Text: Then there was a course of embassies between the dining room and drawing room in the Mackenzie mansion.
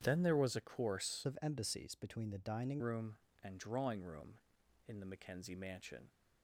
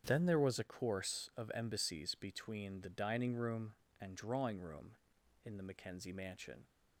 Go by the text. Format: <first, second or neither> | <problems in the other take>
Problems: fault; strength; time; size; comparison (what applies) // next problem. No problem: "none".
second | starts louder than the rest; strong; until 1.0 s; 9 dB; strong in the second // changes voice from "of" to "dining"; from 1.2 to 2.8 s; 1.6 s long